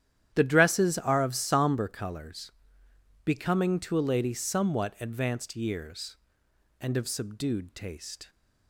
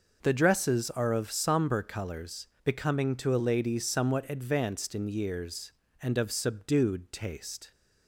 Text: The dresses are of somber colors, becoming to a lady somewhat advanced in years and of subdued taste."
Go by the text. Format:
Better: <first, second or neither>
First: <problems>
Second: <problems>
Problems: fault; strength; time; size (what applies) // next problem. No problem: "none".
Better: second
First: starts louder than the rest; strong; until 1.3 s; 10.5 dB // skips "in"; at 5.5 s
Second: none